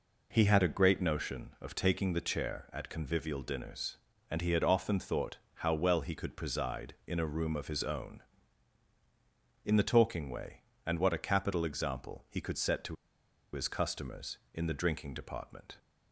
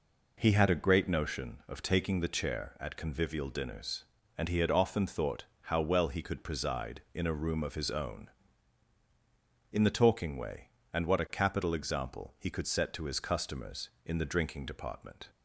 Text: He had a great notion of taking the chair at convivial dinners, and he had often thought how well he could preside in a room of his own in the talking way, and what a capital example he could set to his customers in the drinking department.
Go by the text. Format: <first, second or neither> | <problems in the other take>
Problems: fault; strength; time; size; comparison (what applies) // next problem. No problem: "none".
second | pauses between "thought" and "how"; slight; at 5.3 s; 0.20 s long; slight in the second // pauses between "to" and "his"; noticeable; at 12.9 s; 0.57 s long